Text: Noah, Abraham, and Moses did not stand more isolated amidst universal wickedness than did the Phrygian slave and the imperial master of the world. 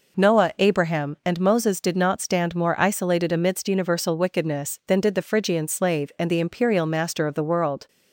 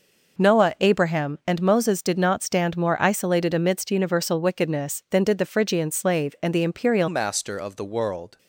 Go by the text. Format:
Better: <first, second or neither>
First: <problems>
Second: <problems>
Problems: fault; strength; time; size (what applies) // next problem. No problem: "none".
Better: first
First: none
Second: changes voice at "master"; from 7.0 s on; 1.3 s long